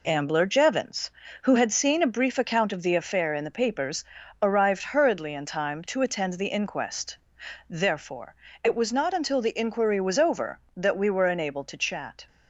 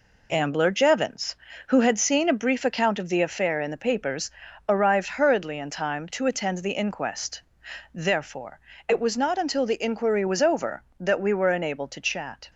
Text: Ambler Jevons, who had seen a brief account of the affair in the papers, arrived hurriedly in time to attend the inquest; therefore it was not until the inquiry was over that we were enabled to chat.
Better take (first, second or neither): neither